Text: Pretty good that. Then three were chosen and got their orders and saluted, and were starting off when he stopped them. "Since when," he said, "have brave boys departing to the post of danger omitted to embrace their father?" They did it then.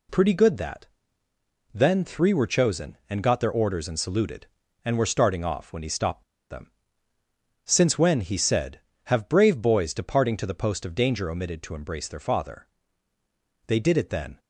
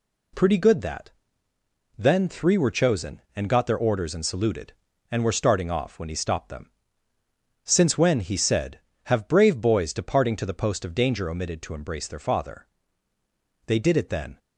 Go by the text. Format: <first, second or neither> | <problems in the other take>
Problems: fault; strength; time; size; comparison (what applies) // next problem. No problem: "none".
second | pauses between "stopped" and "them"; slight; at 6.2 s; 0.27 s long